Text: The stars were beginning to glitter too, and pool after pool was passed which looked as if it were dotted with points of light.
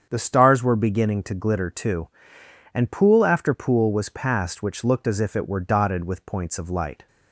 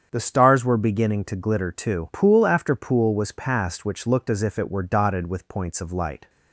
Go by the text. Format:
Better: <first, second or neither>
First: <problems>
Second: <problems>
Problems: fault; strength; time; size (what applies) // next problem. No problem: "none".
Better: first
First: starts louder than the rest; strong; until 1.1 s; 7.5 dB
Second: starts louder than the rest; strong; until 1.1 s; 8 dB // skips "and"; at 2.1 s